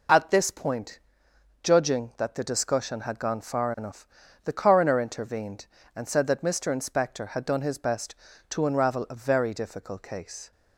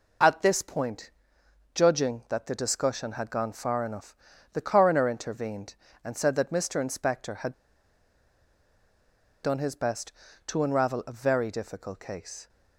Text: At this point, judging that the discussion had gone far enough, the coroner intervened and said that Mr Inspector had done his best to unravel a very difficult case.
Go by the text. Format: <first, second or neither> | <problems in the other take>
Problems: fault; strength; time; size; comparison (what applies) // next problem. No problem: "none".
first | pauses between "had" and "done"; strong; at 7.5 s; 1.8 s long